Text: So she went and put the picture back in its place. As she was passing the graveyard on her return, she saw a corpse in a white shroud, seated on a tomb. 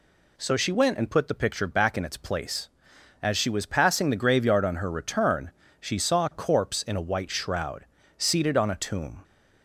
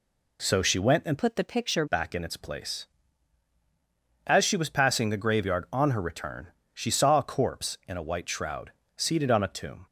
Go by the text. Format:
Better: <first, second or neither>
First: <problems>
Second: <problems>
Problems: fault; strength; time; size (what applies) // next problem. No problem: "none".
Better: first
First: none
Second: changes voice from "put" to "picture"; from 1.1 to 1.8 s; 0.7 s long